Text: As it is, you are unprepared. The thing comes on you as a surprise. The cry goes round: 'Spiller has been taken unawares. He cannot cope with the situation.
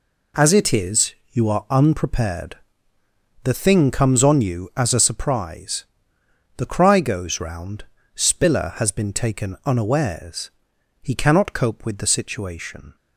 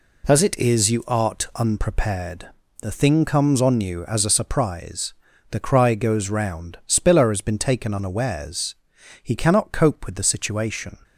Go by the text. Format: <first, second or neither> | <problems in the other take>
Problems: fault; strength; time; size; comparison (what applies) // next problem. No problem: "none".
first | says "art" for "are"; at 1.0 s